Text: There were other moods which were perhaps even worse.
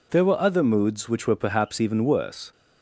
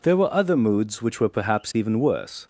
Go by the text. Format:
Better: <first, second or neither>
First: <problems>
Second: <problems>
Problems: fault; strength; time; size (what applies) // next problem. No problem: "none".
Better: neither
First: none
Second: none